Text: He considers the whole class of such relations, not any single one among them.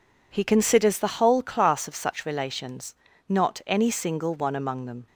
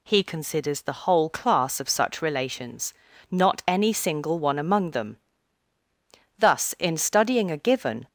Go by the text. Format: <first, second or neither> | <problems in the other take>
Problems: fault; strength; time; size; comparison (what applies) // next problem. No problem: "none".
first | goes on to say "Thus in studying a given"; strong; from 6.3 s on; 1.7 s long